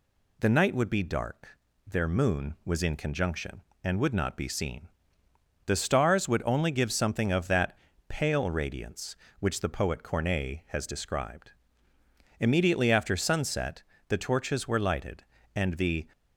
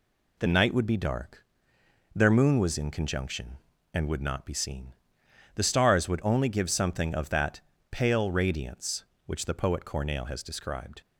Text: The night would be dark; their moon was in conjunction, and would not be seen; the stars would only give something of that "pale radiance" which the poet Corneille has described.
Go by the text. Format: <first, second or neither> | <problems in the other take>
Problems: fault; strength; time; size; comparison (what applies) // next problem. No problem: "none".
second | pauses between "that" and "pale"; slight; at 7.7 s; 0.30 s long; slight in the second // goes on to say "Immediately after sunset the torches were lighted and the"; strong; from 12.4 s on; 3.6 s long